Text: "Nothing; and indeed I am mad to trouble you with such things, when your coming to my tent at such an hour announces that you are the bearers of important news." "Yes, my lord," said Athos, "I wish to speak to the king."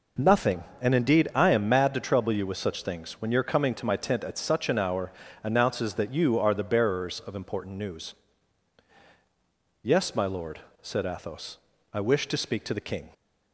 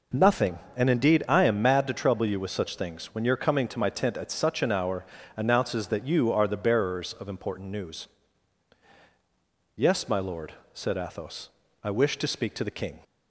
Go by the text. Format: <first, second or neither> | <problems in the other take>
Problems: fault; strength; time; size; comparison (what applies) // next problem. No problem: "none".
neither | pauses between "hour" and "announces"; slight; the same in both